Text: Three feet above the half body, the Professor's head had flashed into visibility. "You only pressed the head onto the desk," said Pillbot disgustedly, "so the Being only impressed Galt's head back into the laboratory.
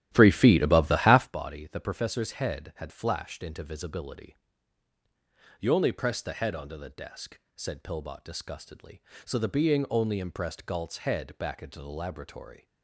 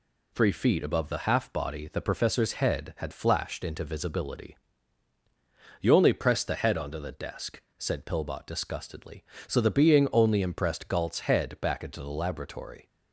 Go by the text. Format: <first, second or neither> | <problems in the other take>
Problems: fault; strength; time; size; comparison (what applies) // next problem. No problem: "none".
second | starts louder than the rest; strong; until 1.3 s; 13 dB